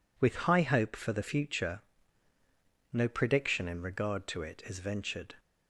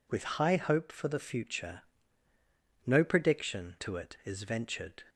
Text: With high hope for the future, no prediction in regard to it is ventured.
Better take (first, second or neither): first